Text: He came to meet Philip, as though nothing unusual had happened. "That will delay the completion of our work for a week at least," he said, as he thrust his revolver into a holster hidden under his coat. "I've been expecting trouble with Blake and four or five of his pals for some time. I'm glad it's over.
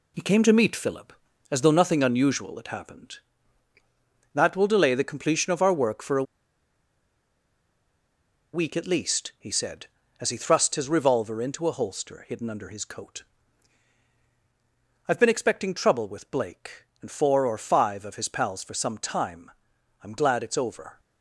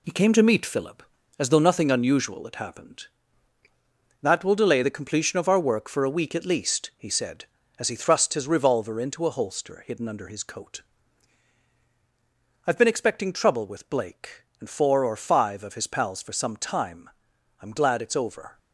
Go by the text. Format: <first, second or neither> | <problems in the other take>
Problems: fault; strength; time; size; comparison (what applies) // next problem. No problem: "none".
second | pauses between "a" and "week"; strong; at 6.2 s; 2.3 s long